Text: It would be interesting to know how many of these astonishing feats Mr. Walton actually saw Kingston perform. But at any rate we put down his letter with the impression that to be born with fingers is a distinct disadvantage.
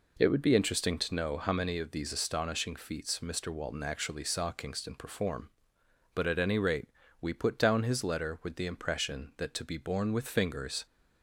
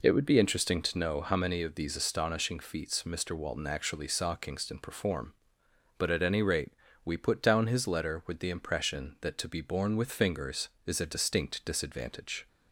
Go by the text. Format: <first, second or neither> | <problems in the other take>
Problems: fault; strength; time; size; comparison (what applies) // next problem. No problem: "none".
second | pauses between "rate" and "we"; slight; at 6.8 s; 0.34 s long; slight in the second // stops before "is a distinct disadvantage"; at 10.8 s